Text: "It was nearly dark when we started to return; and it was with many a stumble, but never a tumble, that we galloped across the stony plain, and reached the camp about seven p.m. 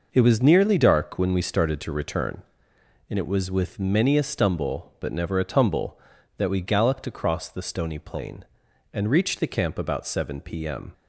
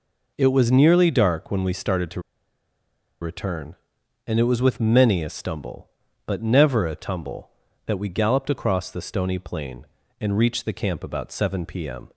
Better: first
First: none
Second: pauses between "to" and "return"; at 2.1 s; 1.0 s long

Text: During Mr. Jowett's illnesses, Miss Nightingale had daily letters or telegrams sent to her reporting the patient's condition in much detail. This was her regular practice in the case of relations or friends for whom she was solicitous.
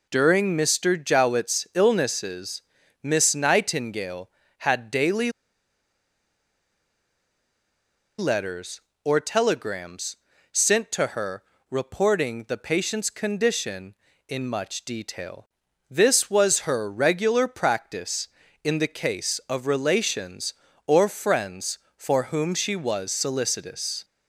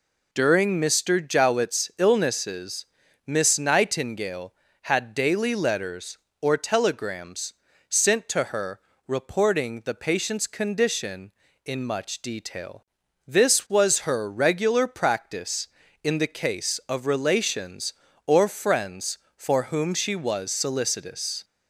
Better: second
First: pauses between "daily" and "letters"; strong; at 5.3 s; 2.8 s long // pauses between "telegrams" and "sent"; slight; at 10.1 s; 0.36 s long // pauses between "her" and "reporting"; slight; at 11.4 s; 0.28 s long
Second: pauses between "telegrams" and "sent"; slight; at 7.5 s; 0.36 s long // pauses between "her" and "reporting"; slight; at 8.7 s; 0.28 s long

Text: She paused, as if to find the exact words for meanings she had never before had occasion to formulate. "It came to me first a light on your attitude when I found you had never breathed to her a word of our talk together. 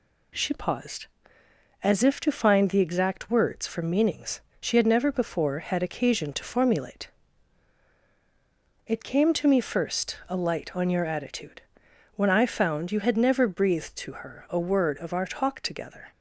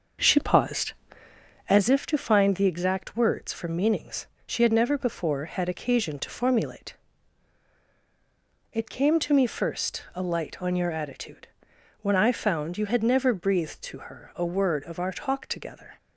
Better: first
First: pauses between "meanings" and "she"; slight; at 4.3 s; 0.20 s long // pauses between "attitude" and "when"; noticeable; at 11.6 s; 0.54 s long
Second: starts louder than the rest; until 1.9 s; 6 dB // pauses between "meanings" and "she"; slight; at 4.2 s; 0.20 s long // pauses between "attitude" and "when"; noticeable; at 11.4 s; 0.54 s long

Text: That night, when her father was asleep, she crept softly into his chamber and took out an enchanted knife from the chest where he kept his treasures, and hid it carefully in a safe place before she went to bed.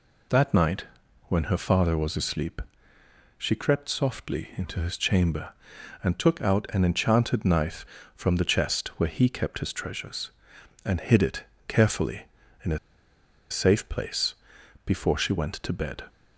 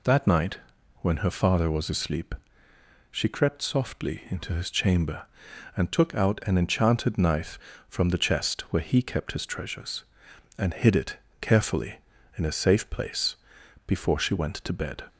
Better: second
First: pauses between "it" and "carefully"; slight; at 11.4 s; 0.24 s long // pauses between "a" and "safe"; noticeable; at 12.7 s; 0.72 s long // pauses between "place" and "before"; noticeable; at 14.3 s; 0.52 s long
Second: pauses between "it" and "carefully"; slight; at 11.1 s; 0.24 s long // pauses between "place" and "before"; noticeable; at 13.3 s; 0.52 s long

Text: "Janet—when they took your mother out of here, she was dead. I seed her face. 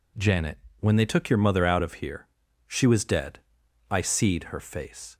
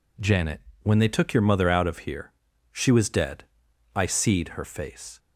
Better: neither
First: none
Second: none

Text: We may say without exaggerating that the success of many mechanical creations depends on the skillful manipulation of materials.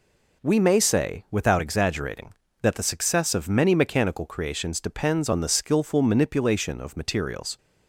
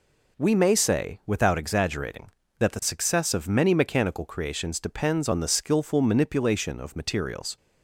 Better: neither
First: none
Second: none

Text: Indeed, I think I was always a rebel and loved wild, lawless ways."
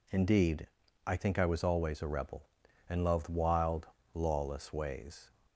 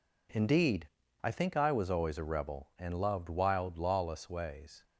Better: neither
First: none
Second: none

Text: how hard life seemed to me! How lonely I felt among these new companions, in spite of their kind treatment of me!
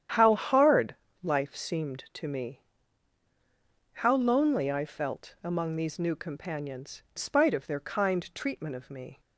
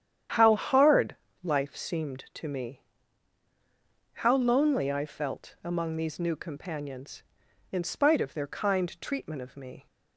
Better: second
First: starts louder than the rest; strong; until 1.4 s; 10 dB // pauses between "hard" and "life"; slight; at 0.9 s; 0.26 s long // skips "in"; at 7.0 s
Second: starts louder than the rest; strong; until 1.6 s; 10 dB // pauses between "hard" and "life"; slight; at 1.1 s; 0.26 s long

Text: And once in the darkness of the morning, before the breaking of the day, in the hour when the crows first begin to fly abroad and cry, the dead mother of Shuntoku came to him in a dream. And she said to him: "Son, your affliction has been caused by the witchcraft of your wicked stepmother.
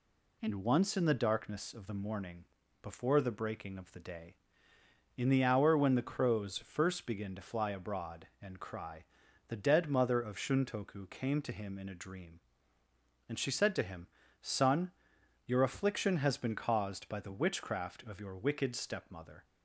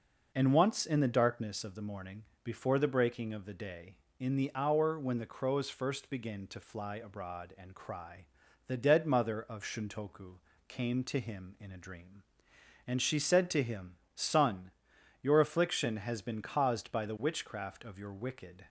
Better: first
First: none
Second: pauses between "Shuntoku" and "came"; slight; at 10.3 s; 0.28 s long // stops before "stepmother"; at 18.6 s

